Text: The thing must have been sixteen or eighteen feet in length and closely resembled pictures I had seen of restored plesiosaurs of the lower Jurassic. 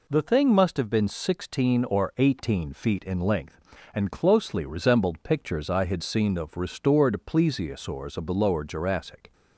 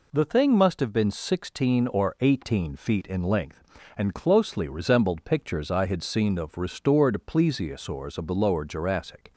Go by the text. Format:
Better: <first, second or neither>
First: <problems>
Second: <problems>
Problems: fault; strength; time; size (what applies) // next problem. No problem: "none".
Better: neither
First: none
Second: none